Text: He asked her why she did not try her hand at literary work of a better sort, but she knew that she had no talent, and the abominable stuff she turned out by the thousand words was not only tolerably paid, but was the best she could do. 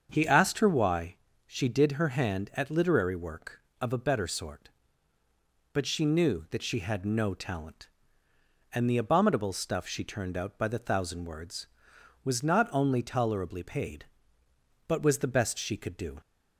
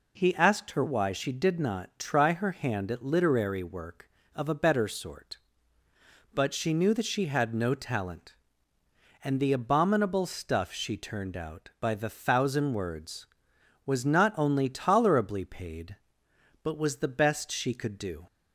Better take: second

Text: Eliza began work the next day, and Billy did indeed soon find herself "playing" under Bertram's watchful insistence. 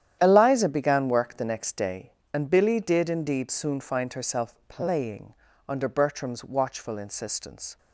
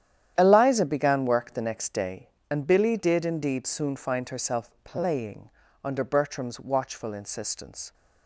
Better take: neither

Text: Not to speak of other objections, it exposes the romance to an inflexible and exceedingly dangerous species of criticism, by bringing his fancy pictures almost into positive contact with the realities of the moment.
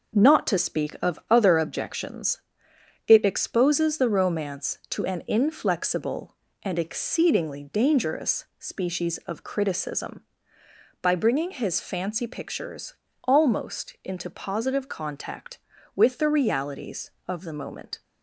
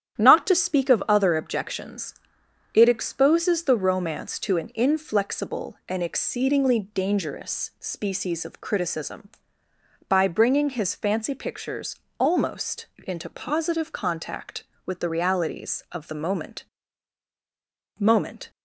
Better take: first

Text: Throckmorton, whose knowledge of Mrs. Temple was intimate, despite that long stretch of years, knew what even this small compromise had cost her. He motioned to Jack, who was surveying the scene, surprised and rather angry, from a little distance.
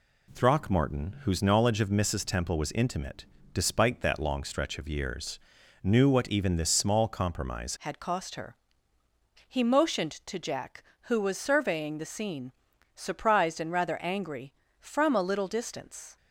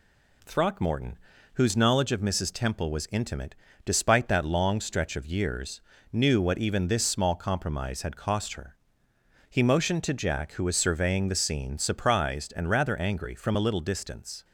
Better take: second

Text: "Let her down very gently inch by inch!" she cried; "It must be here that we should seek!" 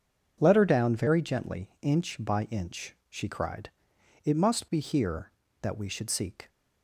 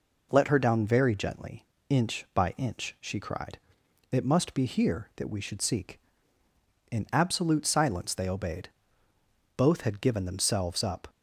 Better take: first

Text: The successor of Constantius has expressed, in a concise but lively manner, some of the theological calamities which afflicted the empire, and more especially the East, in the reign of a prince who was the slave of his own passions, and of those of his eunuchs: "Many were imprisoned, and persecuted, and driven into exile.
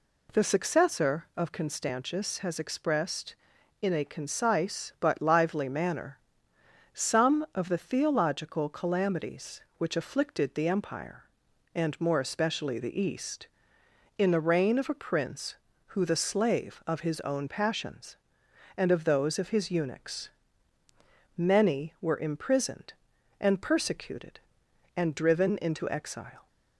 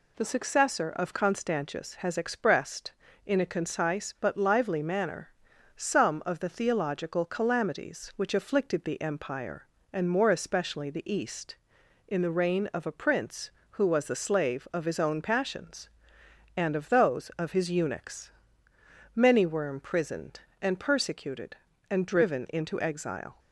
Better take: second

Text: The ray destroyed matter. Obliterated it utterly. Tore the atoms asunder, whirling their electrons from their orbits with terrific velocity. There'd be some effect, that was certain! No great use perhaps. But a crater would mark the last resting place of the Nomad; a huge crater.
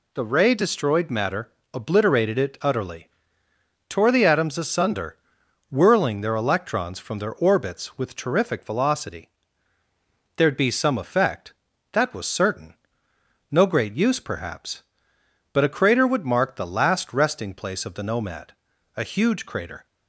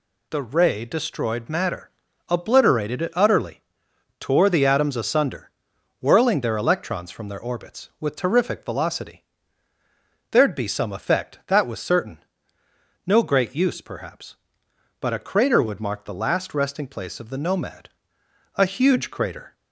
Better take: neither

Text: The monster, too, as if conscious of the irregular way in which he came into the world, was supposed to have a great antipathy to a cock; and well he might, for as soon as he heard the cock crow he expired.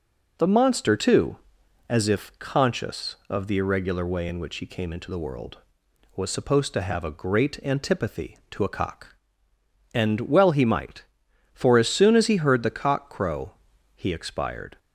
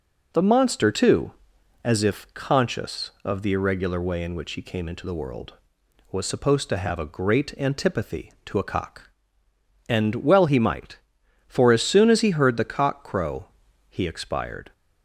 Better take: neither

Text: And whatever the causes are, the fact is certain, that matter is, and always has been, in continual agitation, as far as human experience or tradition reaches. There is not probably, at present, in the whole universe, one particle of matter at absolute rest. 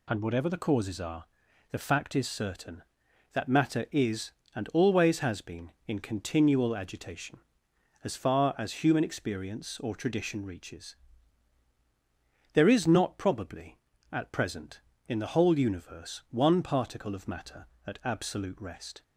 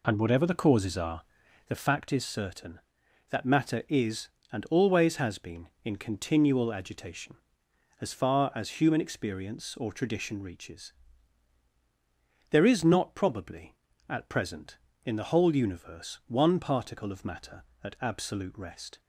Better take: first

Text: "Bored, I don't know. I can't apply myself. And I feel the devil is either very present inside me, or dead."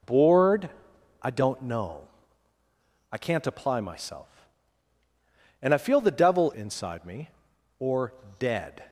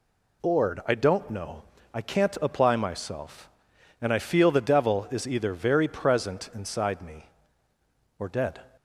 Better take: second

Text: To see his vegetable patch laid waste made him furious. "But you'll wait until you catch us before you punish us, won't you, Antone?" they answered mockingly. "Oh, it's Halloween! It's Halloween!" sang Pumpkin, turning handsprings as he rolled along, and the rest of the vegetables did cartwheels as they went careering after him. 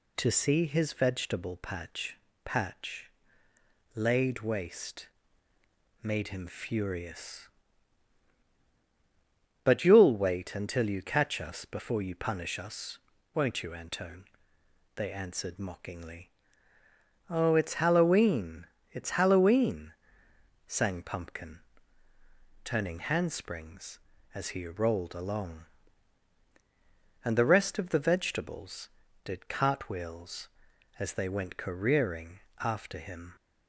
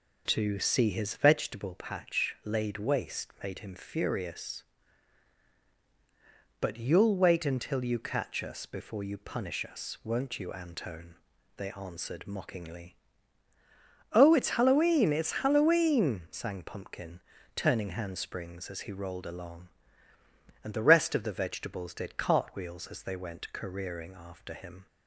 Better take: second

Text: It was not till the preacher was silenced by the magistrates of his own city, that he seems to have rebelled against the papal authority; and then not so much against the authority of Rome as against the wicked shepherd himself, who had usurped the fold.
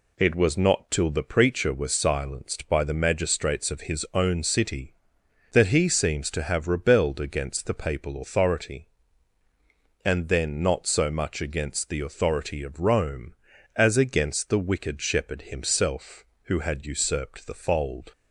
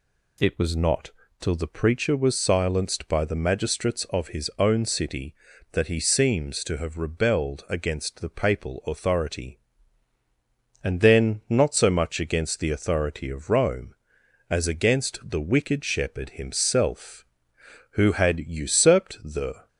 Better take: first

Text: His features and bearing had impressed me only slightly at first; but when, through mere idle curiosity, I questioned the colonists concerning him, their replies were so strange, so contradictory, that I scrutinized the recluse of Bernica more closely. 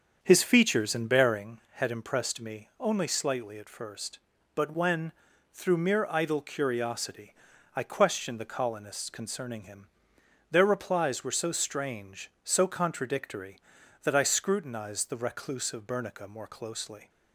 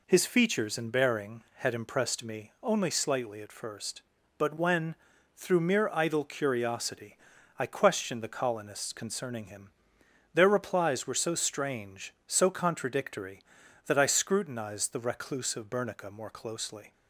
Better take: second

